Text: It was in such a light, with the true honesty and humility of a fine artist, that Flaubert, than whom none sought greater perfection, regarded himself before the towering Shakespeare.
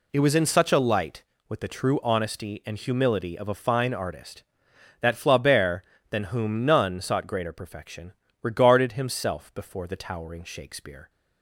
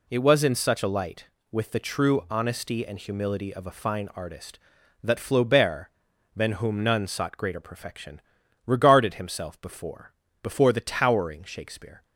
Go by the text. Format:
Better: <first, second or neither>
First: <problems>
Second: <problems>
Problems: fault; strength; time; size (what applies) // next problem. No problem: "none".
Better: first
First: none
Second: says "before" twice; at 10.4 s